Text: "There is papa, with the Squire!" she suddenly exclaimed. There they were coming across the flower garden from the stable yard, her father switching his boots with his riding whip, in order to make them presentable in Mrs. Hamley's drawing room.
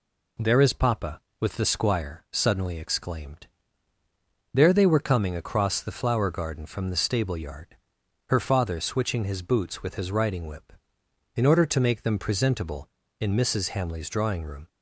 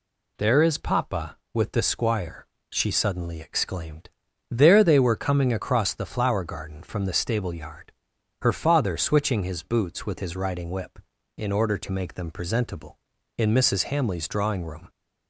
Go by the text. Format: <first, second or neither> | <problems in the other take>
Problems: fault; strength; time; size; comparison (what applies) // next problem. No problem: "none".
second | skips "she"; at 2.2 s